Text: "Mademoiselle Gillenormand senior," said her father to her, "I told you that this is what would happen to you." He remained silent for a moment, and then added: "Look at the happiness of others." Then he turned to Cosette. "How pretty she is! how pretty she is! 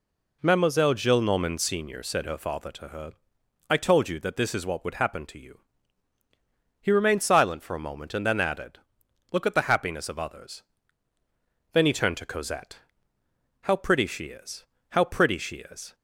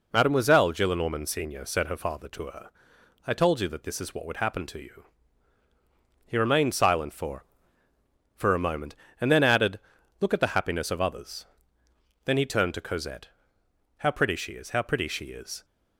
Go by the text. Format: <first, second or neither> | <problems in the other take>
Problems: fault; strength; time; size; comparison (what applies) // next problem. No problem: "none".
first | says "for" twice; at 8.3 s